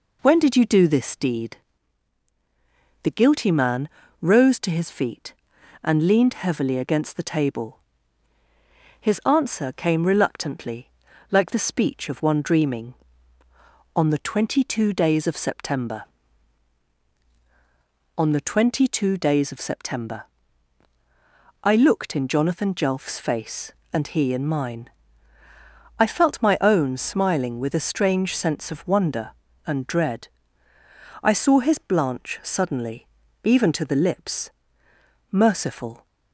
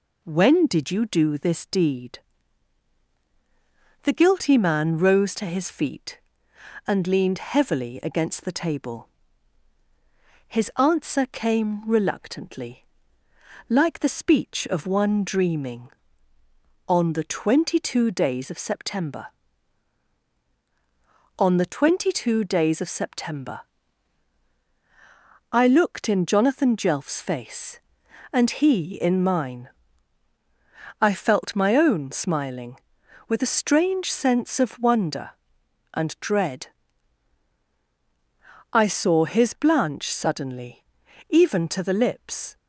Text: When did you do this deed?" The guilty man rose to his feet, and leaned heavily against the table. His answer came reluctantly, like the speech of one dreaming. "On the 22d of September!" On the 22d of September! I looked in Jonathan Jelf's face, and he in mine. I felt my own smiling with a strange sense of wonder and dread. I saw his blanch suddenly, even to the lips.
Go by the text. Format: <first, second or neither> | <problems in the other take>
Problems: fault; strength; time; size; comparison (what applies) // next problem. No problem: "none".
second | pauses between "man" and "rose"; slight; at 3.8 s; 0.34 s long // goes on to say "Merciful"; noticeable; from 35.3 s on; 0.74 s long